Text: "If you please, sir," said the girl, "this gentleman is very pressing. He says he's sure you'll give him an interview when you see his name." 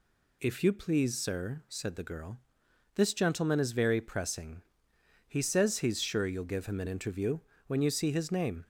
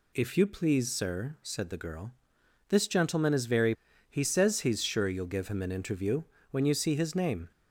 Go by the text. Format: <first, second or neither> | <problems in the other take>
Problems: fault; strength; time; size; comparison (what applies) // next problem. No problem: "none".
first | skips "pressing"; at 3.9 s // pauses between "interview" and "when"; slight; at 6.2 s; 0.26 s long; slight in the first